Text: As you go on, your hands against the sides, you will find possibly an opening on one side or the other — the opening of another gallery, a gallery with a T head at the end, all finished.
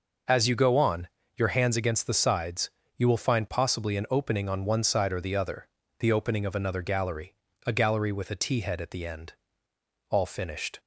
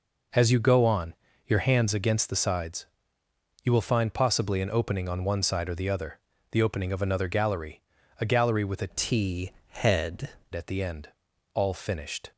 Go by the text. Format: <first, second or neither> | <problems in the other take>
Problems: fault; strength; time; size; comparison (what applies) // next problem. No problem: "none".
first | changes voice from "T" to "head"; from 8.9 to 10.2 s; 1.3 s long // pauses between "T" and "head"; slight; at 9.5 s; 0.18 s long